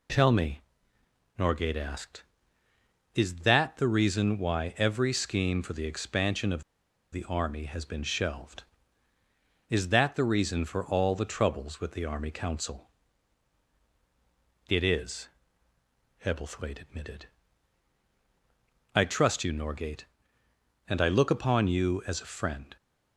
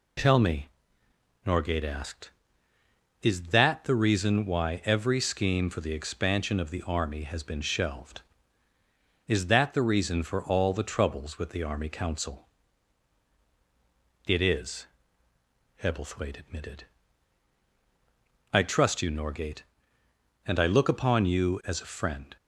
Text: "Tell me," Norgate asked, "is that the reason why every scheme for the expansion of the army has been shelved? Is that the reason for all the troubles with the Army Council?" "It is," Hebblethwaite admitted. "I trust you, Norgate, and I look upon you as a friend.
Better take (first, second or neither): second